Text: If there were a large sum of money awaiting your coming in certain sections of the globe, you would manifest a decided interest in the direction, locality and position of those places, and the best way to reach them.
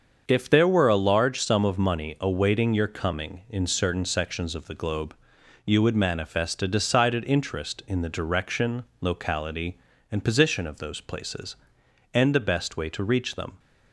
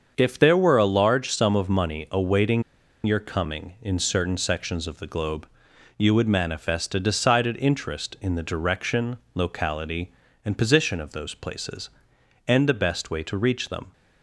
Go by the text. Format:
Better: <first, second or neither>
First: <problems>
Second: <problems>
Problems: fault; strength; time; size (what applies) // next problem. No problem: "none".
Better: first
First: starts louder than the rest; until 1.2 s; 7 dB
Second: starts louder than the rest; until 1.1 s; 7 dB // pauses between "awaiting" and "your"; at 2.6 s; 0.41 s long